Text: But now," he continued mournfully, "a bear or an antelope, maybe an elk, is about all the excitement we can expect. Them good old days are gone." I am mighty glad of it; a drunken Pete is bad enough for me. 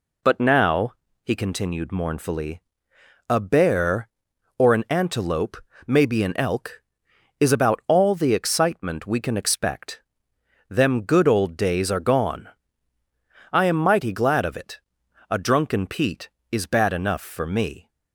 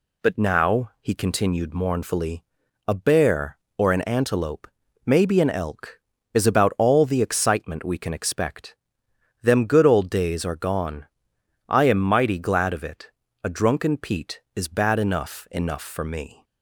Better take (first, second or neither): first